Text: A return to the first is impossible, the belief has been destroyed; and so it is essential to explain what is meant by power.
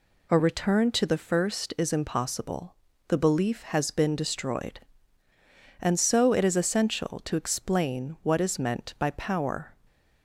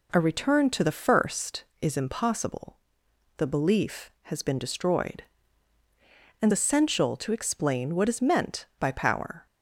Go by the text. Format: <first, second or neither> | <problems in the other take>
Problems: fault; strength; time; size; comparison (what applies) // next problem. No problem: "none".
first | skips "so it is"; at 6.5 s